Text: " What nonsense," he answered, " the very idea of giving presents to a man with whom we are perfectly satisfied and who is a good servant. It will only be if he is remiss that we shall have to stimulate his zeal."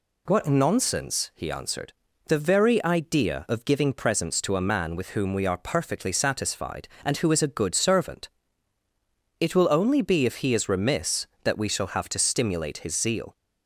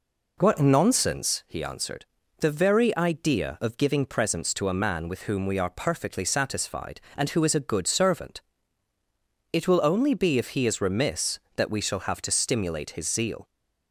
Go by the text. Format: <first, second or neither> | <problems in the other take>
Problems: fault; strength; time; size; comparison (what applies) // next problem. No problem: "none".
first | starts louder than the rest; noticeable; until 1.5 s; 4 dB